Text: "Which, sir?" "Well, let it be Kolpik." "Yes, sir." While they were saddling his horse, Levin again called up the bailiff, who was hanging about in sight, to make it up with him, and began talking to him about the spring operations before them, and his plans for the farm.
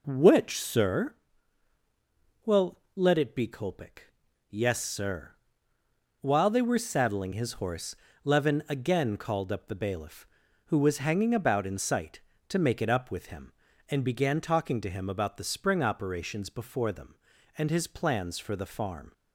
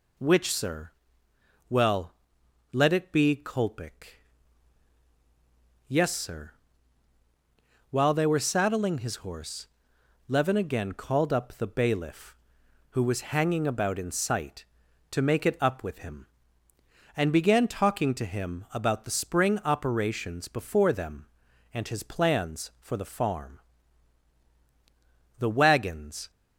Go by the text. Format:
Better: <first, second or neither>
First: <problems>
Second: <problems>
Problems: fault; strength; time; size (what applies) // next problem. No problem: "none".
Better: first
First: none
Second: goes on to say "The wagons"; noticeable; from 25.3 s on; 0.90 s long